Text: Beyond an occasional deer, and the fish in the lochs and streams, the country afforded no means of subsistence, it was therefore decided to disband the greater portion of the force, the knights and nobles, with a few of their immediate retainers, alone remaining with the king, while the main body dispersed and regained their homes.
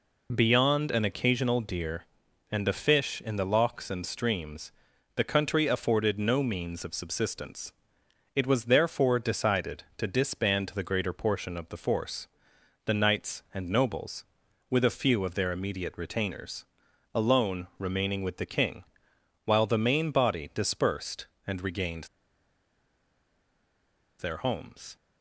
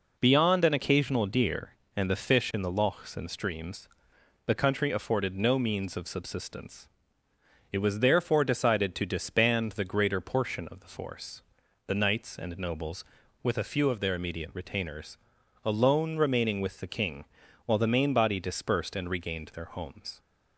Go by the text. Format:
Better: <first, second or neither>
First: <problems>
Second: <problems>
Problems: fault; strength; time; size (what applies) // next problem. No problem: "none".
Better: second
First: pauses between "regained" and "their"; strong; at 22.0 s; 2.1 s long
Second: none